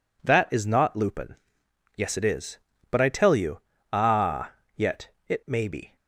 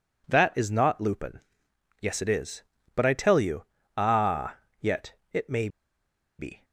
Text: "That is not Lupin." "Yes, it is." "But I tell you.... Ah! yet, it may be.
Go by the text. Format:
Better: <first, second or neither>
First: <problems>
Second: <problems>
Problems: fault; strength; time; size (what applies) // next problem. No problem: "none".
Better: first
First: none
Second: pauses between "may" and "be"; noticeable; at 5.6 s; 0.70 s long